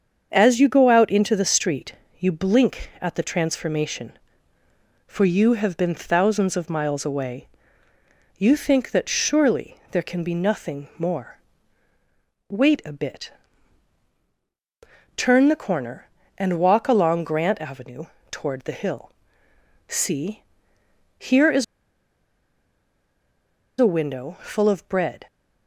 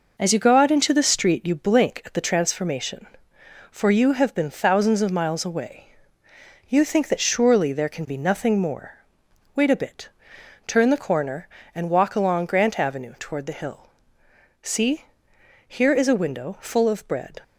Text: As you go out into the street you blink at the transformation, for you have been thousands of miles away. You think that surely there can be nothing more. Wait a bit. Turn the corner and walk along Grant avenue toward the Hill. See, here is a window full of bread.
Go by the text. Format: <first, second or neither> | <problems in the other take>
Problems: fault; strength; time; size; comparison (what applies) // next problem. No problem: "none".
second | starts louder than the rest; until 1.3 s; 7 dB // pauses between "street" and "you"; slight; at 1.9 s; 0.24 s long // pauses between "avenue" and "toward"; slight; at 18.0 s; 0.24 s long // pauses between "is" and "a"; strong; at 21.6 s; 2.1 s long